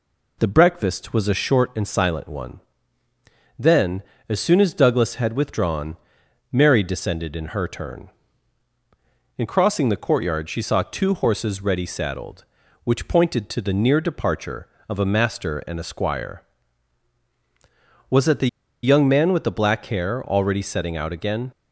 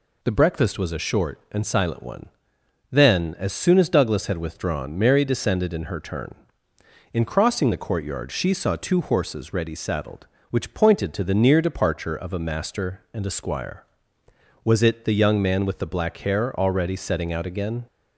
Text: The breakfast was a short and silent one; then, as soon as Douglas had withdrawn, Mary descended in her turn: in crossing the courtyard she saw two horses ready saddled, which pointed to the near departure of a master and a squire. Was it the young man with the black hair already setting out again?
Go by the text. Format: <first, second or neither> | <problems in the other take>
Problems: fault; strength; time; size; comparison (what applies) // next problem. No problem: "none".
second | pauses between "the" and "young"; slight; at 18.4 s; 0.36 s long